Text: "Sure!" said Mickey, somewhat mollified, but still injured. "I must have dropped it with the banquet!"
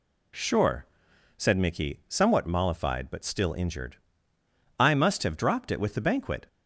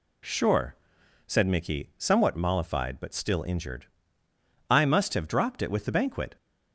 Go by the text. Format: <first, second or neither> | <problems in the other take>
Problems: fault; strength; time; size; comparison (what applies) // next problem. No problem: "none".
neither | none